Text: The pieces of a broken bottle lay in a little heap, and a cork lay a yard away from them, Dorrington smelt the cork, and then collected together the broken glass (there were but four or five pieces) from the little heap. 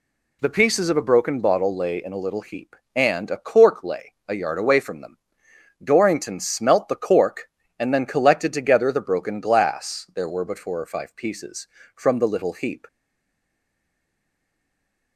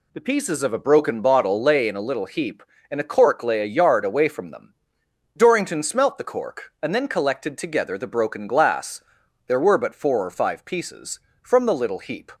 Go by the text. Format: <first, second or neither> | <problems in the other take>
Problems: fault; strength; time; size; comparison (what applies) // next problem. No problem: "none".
second | pauses between "lay" and "a"; slight; at 4.1 s; 0.16 s long // stays silent after the last word; from 12.8 s on; 2.3 s long